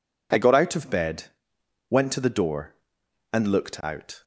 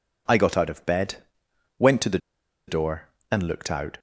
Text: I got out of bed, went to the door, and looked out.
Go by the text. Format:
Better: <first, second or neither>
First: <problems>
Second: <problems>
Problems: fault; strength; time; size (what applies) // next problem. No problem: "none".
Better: first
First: none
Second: pauses between "the" and "door"; noticeable; at 2.1 s; 0.50 s long